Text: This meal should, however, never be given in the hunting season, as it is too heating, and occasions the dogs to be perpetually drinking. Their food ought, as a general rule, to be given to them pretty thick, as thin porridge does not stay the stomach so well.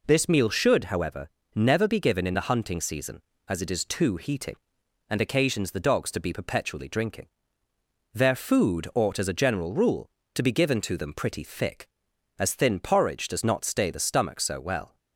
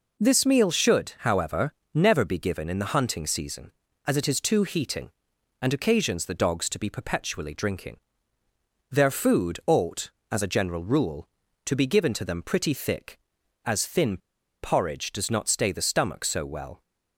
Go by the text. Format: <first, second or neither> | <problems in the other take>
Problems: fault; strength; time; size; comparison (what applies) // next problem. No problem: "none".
first | pauses between "thin" and "porridge"; at 14.1 s; 0.45 s long